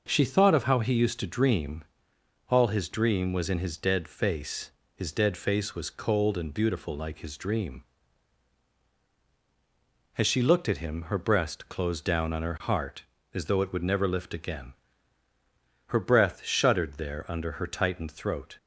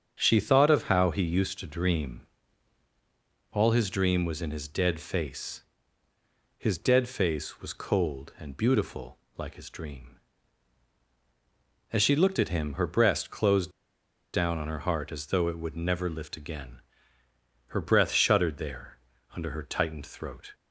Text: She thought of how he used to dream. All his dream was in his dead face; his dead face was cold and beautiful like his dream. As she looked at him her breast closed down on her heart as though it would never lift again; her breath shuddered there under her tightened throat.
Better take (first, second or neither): first